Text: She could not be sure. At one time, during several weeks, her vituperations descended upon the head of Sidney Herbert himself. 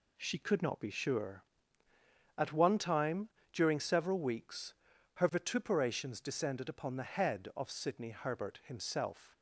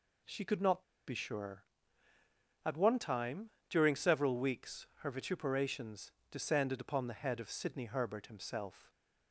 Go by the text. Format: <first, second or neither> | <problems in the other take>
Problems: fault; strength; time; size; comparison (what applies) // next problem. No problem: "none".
first | pauses between "not" and "be"; slight; at 0.8 s; 0.24 s long // pauses between "vituperations" and "descended"; slight; at 6.0 s; 0.20 s long